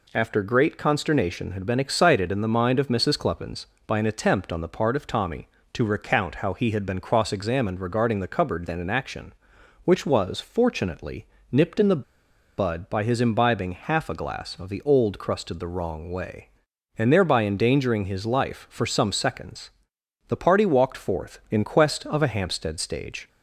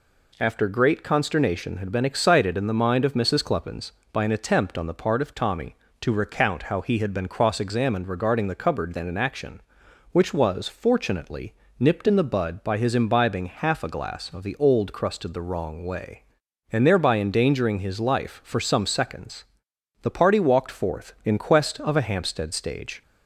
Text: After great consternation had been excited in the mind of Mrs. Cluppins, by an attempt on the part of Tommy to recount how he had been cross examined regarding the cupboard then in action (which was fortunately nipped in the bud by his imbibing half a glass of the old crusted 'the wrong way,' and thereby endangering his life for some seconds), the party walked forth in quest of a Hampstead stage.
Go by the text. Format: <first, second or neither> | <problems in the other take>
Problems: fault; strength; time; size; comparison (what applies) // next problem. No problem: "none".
second | pauses between "fortunately" and "nipped"; slight; at 11.2 s; 0.26 s long; slight in the second // pauses between "the" and "bud"; noticeable; at 12.0 s; 0.55 s long